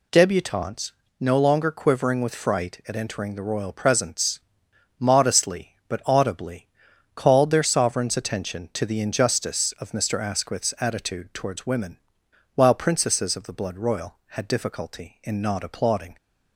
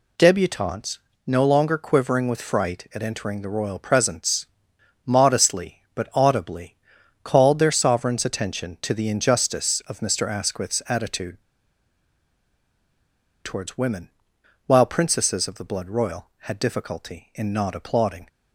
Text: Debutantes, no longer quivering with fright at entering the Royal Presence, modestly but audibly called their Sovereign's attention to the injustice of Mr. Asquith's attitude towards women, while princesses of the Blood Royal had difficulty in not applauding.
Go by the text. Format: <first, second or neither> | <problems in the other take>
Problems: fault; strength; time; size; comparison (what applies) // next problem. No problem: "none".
first | pauses between "audibly" and "called"; noticeable; at 6.7 s; 0.48 s long; noticeable in the first // pauses between "attitude" and "towards"; strong; at 11.4 s; 2.0 s long